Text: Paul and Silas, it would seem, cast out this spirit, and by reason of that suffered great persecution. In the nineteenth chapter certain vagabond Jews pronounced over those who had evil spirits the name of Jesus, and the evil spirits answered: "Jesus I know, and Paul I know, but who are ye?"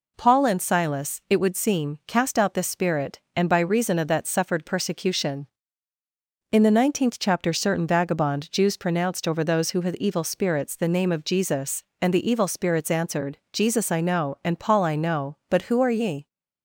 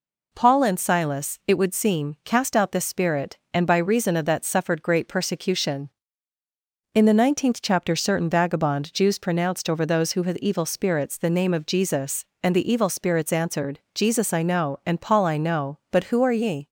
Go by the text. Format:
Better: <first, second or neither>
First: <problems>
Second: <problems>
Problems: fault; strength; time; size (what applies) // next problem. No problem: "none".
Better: second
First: skips "great"; at 4.6 s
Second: none